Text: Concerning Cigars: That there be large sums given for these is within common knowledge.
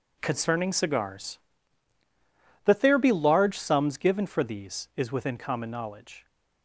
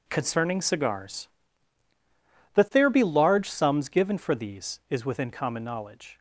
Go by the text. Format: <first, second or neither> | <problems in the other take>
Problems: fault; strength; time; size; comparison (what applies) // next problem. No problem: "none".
neither | none